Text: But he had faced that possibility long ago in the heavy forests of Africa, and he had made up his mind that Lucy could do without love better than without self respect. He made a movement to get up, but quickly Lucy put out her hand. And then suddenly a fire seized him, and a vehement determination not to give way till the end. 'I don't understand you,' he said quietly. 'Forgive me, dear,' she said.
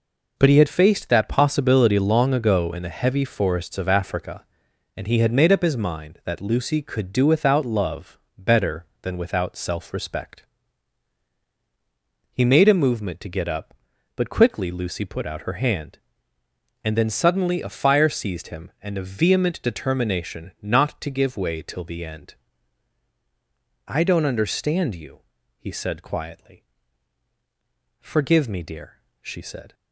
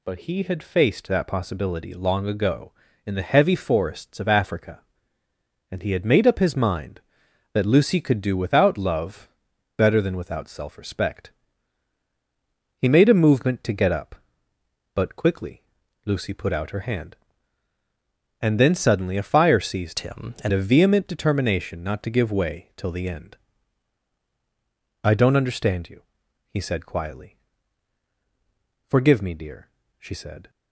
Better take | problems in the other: first | pauses between "love" and "better"; noticeable; at 9.2 s; 0.48 s long; slight in the first // pauses between "quickly" and "Lucy"; at 15.6 s; 0.42 s long // changes voice from "him" to "and"; from 19.9 to 20.5 s; 0.6 s long

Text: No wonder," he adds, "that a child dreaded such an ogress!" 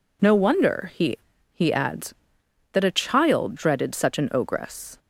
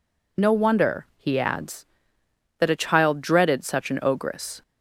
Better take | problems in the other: second | says "he" twice; at 1.5 s

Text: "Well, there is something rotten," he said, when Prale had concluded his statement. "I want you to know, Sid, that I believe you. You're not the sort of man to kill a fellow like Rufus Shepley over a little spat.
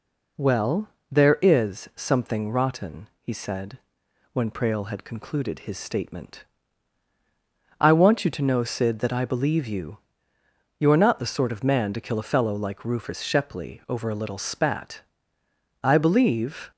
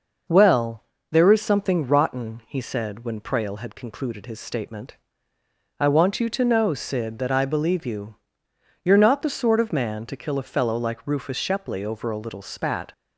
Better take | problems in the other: second | goes on to say "I believe"; noticeable; from 15.8 s on; 0.88 s long

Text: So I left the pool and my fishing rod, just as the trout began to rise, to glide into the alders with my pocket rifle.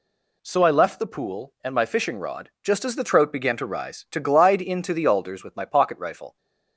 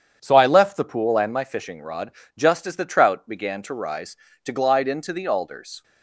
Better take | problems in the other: first | starts louder than the rest; strong; until 1.2 s; 8 dB // stops before "with my pocket rifle"; at 5.8 s

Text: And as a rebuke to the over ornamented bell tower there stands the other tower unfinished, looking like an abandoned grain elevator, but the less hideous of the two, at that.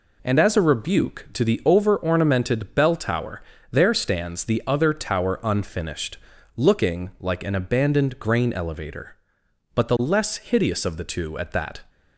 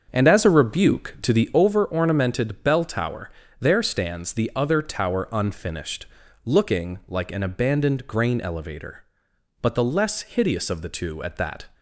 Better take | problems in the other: first | starts louder than the rest; until 1.7 s; 6.5 dB // pauses between "tower" and "there"; slight; at 3.2 s; 0.32 s long; slight in the first

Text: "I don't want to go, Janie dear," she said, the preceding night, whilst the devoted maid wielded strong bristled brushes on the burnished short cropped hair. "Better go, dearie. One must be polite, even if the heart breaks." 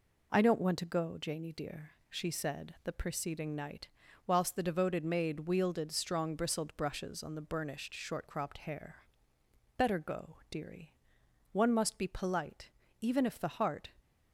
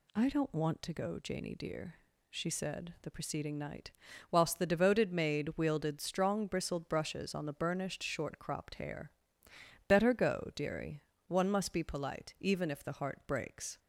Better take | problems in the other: second | stops before "breaks"; at 13.9 s

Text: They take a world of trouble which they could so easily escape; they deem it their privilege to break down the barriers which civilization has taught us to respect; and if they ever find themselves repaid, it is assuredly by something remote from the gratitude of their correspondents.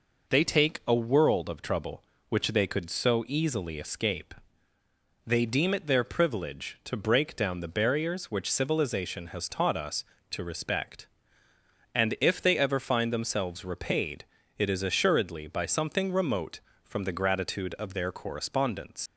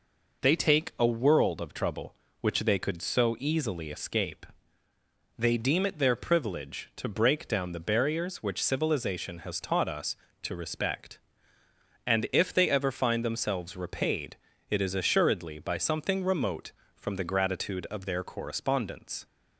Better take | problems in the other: second | leaves "correspondents" unfinished; at 19.0 s; 75 ms

